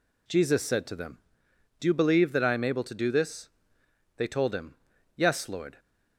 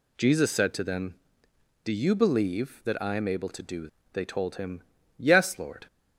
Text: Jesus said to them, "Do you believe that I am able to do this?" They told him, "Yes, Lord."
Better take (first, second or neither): first